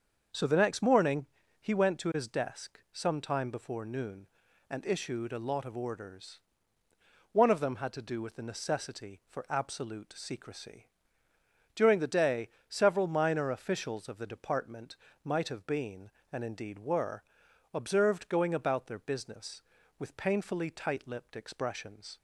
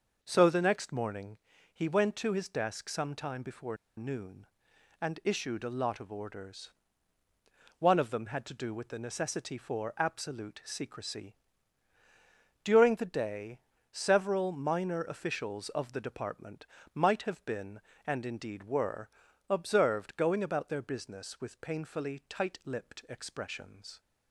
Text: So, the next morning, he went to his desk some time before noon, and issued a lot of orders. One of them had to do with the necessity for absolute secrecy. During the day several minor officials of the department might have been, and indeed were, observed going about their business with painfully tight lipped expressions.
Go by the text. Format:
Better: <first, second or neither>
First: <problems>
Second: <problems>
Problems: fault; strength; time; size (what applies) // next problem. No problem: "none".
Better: first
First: starts louder than the rest; until 1.6 s; 6.5 dB // pauses between "day" and "several"; slight; at 12.4 s; 0.18 s long // pauses between "department" and "might"; slight; at 14.9 s; 0.28 s long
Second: starts louder than the rest; noticeable; until 1.2 s; 6 dB // pauses between "before" and "noon"; slight; at 3.7 s; 0.21 s long // pauses between "day" and "several"; slight; at 13.5 s; 0.36 s long // pauses between "department" and "might"; slight; at 16.6 s; 0.30 s long